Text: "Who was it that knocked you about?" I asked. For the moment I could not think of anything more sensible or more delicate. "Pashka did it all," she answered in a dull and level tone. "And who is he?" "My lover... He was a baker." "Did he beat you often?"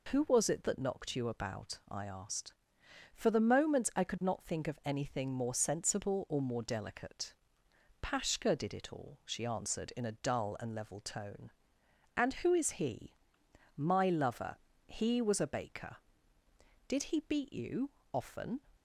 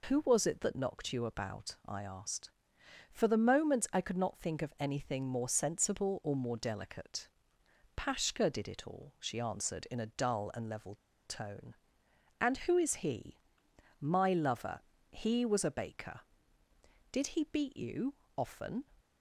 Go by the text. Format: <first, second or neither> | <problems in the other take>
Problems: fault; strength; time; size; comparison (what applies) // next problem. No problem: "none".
first | pauses between "level" and "tone"; slight; at 10.9 s; 0.31 s long // pauses between "you" and "often"; slight; at 18.1 s; 0.20 s long; slight in the first